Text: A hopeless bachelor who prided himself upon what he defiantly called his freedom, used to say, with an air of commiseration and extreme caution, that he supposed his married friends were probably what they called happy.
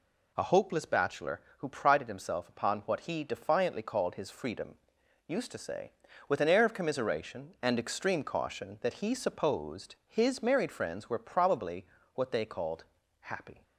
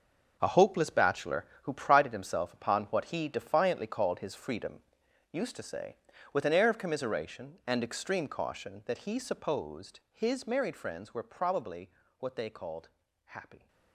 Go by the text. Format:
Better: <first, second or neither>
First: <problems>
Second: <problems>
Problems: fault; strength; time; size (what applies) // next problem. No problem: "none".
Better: first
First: pauses between "probably" and "what"; slight; at 11.8 s; 0.30 s long // pauses between "called" and "happy"; slight; at 12.8 s; 0.36 s long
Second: gets quieter; strong; throughout; 11.5 dB // pauses between "probably" and "what"; slight; at 11.8 s; 0.30 s long // pauses between "called" and "happy"; slight; at 12.8 s; 0.36 s long